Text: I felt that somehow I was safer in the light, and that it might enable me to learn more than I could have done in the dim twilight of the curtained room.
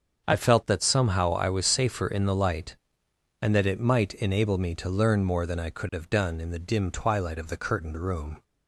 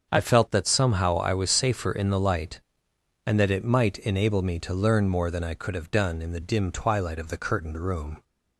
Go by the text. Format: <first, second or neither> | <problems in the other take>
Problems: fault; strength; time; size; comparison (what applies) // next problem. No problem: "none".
neither | starts louder than the rest; the same in both